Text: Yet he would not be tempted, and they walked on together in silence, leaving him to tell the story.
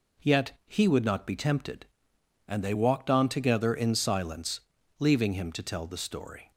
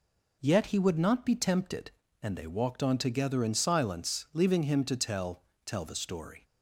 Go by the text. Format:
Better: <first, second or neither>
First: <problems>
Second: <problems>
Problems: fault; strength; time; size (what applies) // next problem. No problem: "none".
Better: first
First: none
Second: says "tell" twice; at 5.6 s